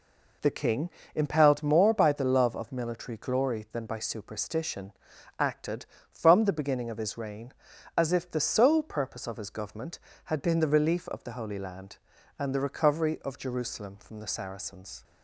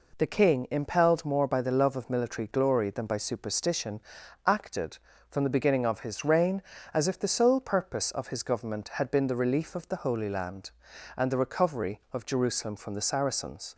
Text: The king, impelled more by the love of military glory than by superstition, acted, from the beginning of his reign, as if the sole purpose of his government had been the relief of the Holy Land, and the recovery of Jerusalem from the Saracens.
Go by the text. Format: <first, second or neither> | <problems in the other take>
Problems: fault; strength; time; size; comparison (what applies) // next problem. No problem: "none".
neither | none